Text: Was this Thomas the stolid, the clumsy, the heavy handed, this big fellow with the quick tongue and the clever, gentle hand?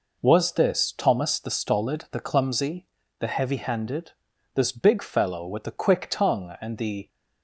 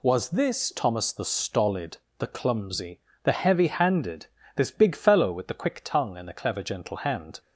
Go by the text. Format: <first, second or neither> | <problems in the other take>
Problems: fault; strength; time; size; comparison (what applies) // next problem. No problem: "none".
second | stops before "clever gentle hand"; at 7.0 s